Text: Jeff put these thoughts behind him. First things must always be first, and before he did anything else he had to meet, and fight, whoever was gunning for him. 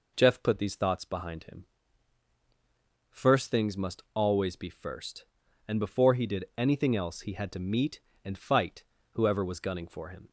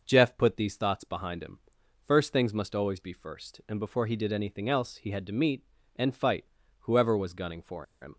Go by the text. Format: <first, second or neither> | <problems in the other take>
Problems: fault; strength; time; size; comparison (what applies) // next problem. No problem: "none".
first | pauses between "for" and "him"; slight; at 7.8 s; 0.17 s long